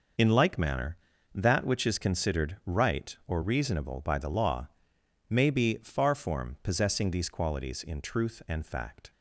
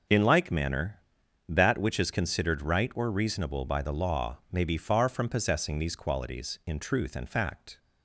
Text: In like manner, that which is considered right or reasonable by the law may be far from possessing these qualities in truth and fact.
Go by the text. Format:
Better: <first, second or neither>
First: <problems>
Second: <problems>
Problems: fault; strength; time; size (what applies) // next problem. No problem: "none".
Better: second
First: pauses between "law" and "may"; noticeable; at 4.6 s; 0.62 s long // says "form" for "from"; at 6.1 s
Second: none